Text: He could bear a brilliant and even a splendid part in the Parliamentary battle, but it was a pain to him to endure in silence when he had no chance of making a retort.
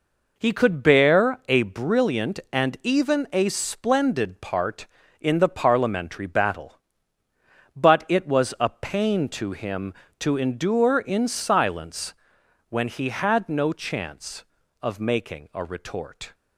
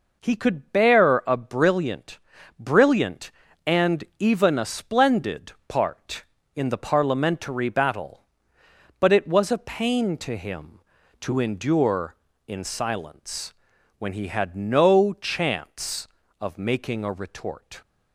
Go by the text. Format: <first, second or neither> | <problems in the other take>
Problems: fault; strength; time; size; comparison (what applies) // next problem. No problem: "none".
first | says "brilliant" twice; at 2.5 s // pauses between "splendid" and "part"; slight; at 5.5 s; 0.16 s long // pauses between "silence" and "when"; noticeable; at 13.5 s; 0.46 s long; noticeable in the first